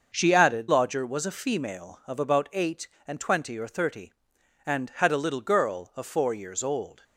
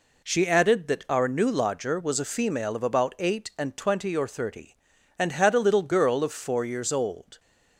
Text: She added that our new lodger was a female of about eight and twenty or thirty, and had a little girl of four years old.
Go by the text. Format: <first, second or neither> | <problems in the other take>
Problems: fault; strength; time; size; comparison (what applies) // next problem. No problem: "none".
second | starts louder than the rest; until 1.1 s; 6.5 dB // skips "that our new"; at 0.6 s